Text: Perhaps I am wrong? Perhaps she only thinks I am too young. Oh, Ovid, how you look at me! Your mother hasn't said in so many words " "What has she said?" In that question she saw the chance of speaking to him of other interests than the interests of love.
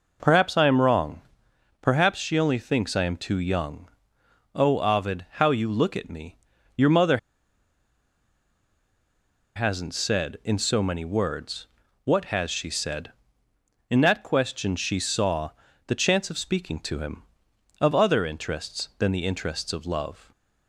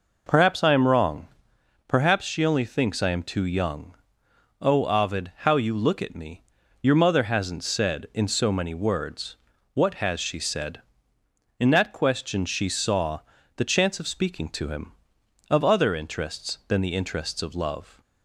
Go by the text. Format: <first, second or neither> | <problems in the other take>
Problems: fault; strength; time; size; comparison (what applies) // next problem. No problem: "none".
second | pauses between "mother" and "hasn't"; strong; at 7.1 s; 2.3 s long // pauses between "saw" and "the"; slight; at 15.5 s; 0.34 s long; slight in the second